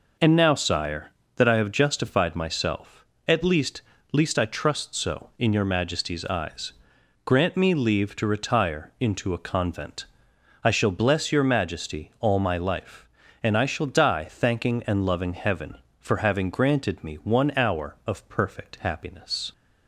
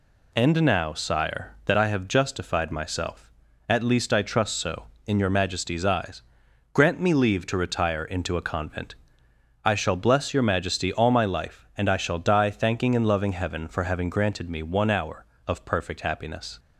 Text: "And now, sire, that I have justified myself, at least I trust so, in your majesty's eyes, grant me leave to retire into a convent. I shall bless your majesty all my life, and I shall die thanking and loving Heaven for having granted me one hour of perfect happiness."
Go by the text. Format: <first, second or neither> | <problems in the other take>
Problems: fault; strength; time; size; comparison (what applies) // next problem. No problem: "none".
second | says "least" twice; at 4.1 s